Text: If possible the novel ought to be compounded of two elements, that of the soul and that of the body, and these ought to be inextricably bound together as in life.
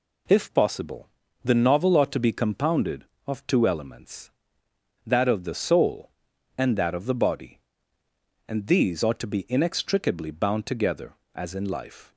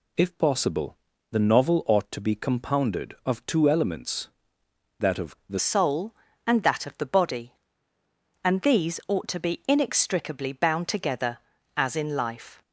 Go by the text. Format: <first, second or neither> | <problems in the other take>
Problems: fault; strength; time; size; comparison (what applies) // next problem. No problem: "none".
first | pauses between "possible" and "the"; slight; at 0.9 s; 0.34 s long; slight in the first // changes voice at "soul"; from 5.5 s on; 7.1 s long